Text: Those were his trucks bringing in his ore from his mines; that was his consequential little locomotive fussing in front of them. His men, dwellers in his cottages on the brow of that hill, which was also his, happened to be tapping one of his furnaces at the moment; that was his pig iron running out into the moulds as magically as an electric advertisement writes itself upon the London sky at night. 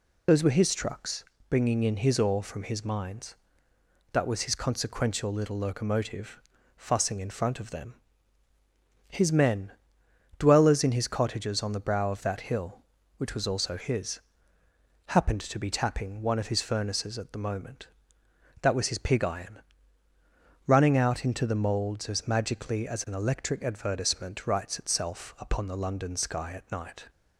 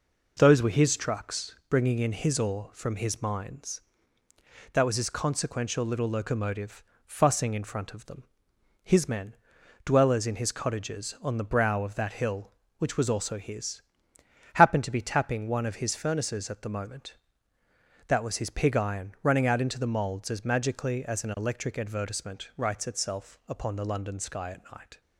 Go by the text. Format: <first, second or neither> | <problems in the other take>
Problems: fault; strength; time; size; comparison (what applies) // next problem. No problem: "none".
second | loses the start of "Those"; at 0.2 s; 50 ms // pauses between "trucks" and "bringing"; slight; at 1.2 s; 0.26 s long // pauses between "locomotive" and "fussing"; at 6.3 s; 0.38 s long; slight in the second // pauses between "iron" and "running"; at 19.6 s; 1.0 s long